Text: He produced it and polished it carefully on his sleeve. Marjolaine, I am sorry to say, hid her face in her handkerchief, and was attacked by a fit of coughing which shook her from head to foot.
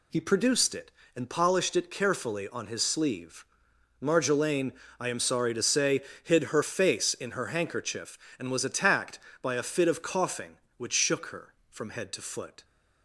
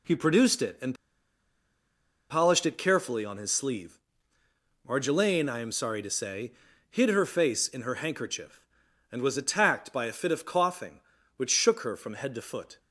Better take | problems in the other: first | pauses between "and" and "polished"; strong; at 0.9 s; 1.3 s long

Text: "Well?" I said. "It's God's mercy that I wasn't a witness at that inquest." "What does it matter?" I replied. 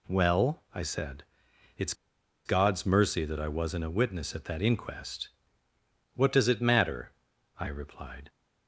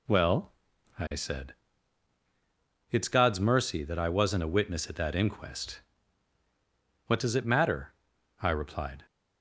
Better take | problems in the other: second | pauses between "It's" and "God's"; noticeable; at 1.9 s; 0.52 s long

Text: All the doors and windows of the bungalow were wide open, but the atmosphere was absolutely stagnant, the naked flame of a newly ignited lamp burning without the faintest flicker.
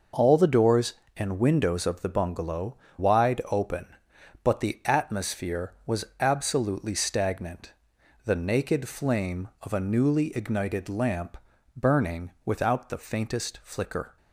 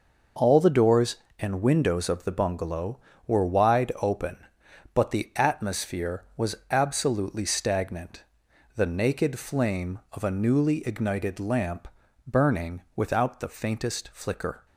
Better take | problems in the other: second | skips "were"; at 2.8 s // pauses between "lamp" and "burning"; at 11.3 s; 0.40 s long; also in the second

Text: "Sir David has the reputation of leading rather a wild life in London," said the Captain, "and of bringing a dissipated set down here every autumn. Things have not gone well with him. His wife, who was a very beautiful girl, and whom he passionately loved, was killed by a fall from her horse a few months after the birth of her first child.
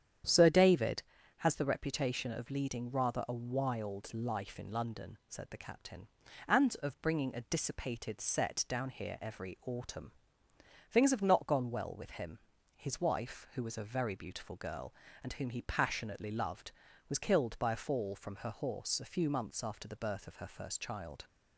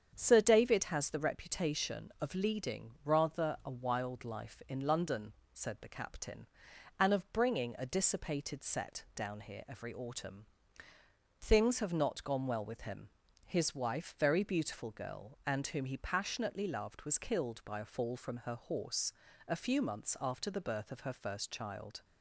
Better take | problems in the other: first | starts louder than the rest; strong; until 1.1 s; 7.5 dB; strong in the first // skips "who was a"; at 14.1 s // pauses between "horse" and "a"; slight; at 19.1 s; 0.36 s long

